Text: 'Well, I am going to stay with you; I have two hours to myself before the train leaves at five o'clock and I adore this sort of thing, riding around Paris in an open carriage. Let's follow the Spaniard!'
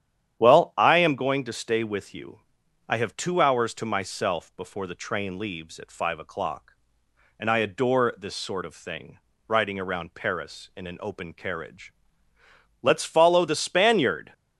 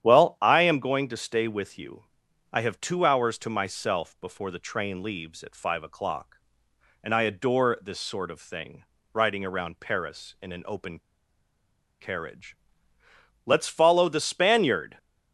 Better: first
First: starts louder than the rest; strong; until 1.4 s; 10 dB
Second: starts louder than the rest; strong; until 1.1 s; 10 dB // pauses between "open" and "carriage"; at 10.9 s; 0.99 s long

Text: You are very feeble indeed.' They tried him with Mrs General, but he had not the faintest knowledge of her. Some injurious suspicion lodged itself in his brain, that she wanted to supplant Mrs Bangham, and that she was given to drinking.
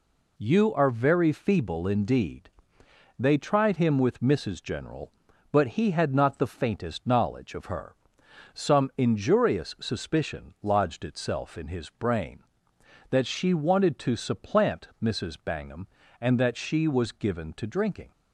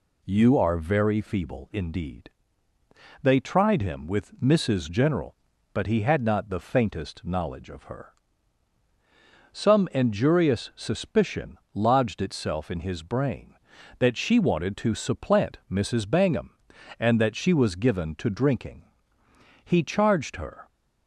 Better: first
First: none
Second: pauses between "suspicion" and "lodged"; slight; at 11.5 s; 0.18 s long // goes on to say "He charged her"; noticeable; from 19.6 s on; 1.0 s long

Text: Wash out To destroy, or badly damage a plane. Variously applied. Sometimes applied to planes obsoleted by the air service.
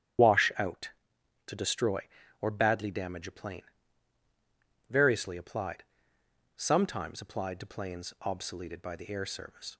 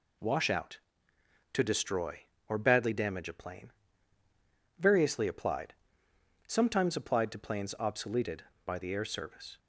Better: second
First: loses the start of "Wash"; at 0.1 s; 40 ms // starts louder than the rest; strong; until 1.8 s; 10 dB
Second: none

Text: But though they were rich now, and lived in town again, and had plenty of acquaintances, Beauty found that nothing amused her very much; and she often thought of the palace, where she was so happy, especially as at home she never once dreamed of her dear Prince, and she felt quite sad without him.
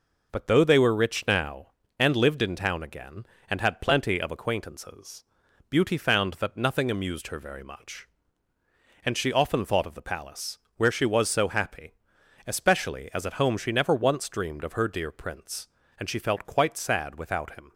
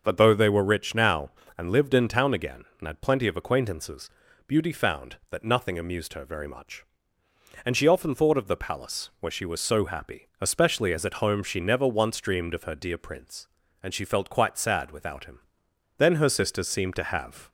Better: first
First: none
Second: starts louder than the rest; until 1.0 s; 6 dB // goes on to say "Then her sisters seemed to have"; from 15.9 s on; 1.5 s long

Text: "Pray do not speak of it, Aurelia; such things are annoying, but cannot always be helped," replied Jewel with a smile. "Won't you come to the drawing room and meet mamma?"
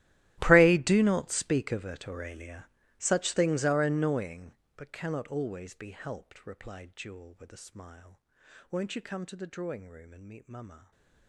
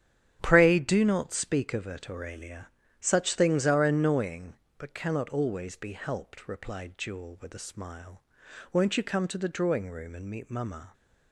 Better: second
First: gets quieter; strong; throughout; 21 dB // starts louder than the rest; strong; until 1.4 s; 14.5 dB // stays silent after the last word; slight; from 10.7 s on; 0.5 s long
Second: starts louder than the rest; strong; until 1.4 s; 9.5 dB

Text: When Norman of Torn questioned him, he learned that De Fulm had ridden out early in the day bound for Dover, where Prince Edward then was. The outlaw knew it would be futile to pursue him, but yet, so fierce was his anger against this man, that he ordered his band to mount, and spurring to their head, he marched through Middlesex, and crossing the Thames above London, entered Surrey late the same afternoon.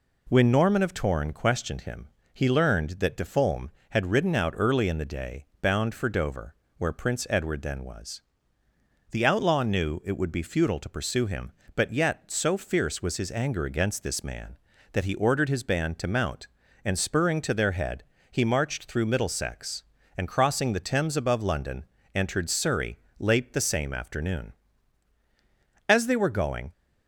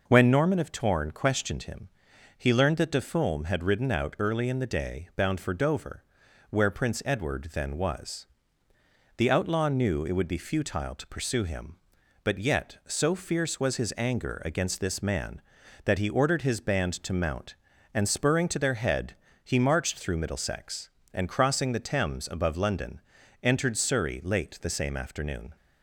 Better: second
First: pauses between "day" and "bound"; slight; at 5.4 s; 0.16 s long // pauses between "Surrey" and "late"; slight; at 22.9 s; 0.20 s long // goes on to say "As they were going"; noticeable; from 25.8 s on; 0.84 s long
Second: none

